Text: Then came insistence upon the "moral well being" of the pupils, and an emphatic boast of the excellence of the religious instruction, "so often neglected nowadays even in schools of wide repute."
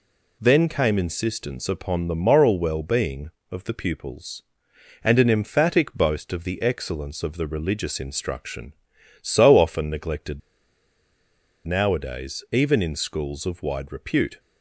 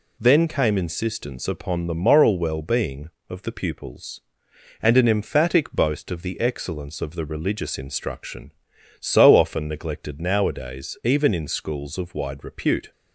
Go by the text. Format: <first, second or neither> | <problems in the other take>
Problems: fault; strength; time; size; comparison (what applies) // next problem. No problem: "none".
second | pauses between "neglected" and "nowadays"; strong; at 10.4 s; 1.2 s long